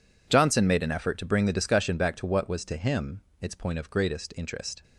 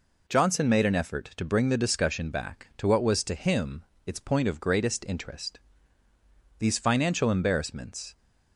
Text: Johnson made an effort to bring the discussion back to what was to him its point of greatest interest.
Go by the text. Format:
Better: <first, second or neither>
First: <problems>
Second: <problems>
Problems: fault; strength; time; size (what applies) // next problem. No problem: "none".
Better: first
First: pauses between "him" and "its"; slight; at 3.2 s; 0.18 s long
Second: pauses between "him" and "its"; slight; at 3.8 s; 0.20 s long // goes on to say "These financial embarrassments"; from 6.5 s on; 1.5 s long